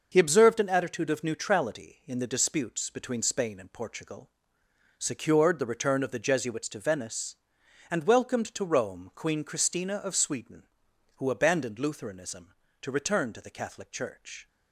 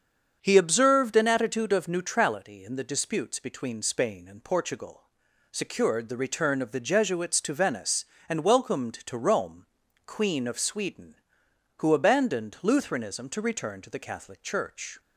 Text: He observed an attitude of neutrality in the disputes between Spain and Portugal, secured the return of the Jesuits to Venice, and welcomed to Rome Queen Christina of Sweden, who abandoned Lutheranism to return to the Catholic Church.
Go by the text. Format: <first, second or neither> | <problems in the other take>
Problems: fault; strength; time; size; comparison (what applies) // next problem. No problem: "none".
first | starts louder than the rest; strong; until 1.4 s; 7 dB // pauses between "Rome" and "Queen"; at 9.6 s; 0.40 s long // skips "Christina"; at 10.4 s